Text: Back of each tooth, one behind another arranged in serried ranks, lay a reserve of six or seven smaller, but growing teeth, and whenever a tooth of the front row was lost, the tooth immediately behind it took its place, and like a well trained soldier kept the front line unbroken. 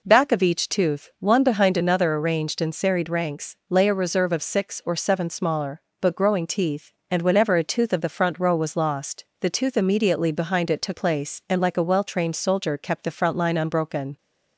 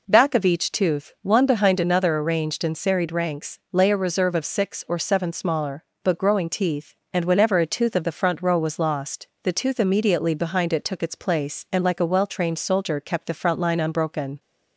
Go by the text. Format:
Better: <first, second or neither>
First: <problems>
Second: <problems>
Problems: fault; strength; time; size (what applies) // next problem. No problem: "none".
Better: second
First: skips "its"; at 10.9 s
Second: none